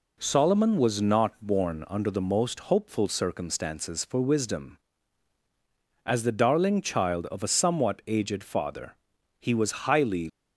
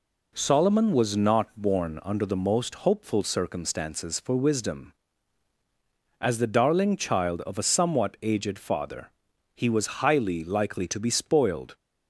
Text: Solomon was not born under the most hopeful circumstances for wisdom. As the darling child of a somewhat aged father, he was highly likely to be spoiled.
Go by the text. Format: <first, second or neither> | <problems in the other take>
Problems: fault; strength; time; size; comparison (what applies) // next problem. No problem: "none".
second | stops before "likely to be spoiled"; at 10.2 s